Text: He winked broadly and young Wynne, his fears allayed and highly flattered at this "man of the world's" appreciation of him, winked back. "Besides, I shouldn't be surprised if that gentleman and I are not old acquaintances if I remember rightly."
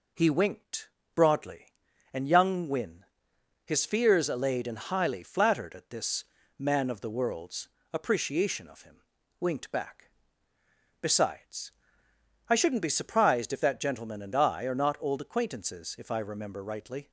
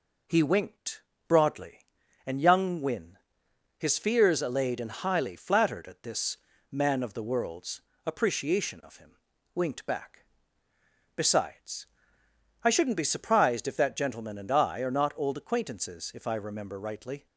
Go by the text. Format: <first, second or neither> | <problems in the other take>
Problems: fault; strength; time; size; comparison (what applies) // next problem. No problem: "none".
neither | pauses between "winked" and "broadly"; slight; the same in both // pauses between "this" and "man"; slight; the same in both // pauses between "world's" and "appreciation"; slight; the same in both